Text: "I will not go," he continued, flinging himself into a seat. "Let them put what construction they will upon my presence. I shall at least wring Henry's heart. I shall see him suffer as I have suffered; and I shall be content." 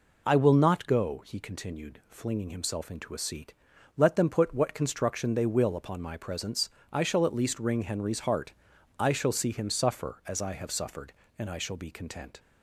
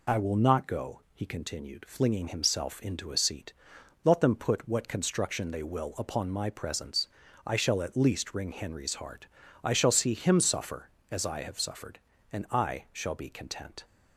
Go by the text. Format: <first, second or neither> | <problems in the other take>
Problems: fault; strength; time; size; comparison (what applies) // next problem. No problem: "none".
neither | none